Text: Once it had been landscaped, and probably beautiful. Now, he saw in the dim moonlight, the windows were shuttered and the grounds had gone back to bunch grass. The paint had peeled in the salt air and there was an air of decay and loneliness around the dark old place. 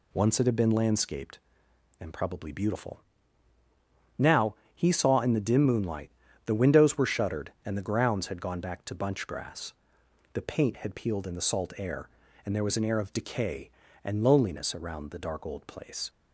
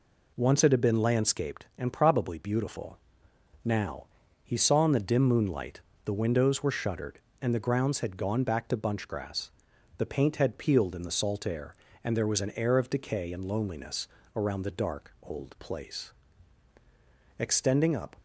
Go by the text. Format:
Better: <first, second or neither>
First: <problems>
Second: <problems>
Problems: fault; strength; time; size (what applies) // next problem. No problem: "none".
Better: first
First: none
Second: pauses between "loneliness" and "around"; slight; at 14.0 s; 0.28 s long // goes on to say "Extending up"; noticeable; from 17.3 s on; 0.78 s long